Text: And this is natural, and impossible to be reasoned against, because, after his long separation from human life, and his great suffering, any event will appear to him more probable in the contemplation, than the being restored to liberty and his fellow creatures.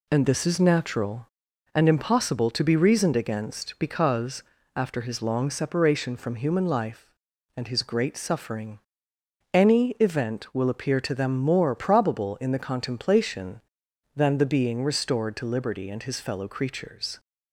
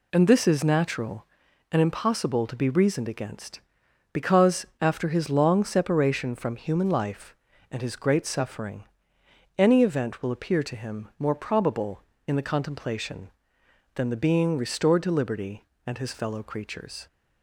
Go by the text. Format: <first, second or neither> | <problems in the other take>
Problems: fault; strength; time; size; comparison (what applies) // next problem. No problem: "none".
second | says "them" for "him"; at 11.1 s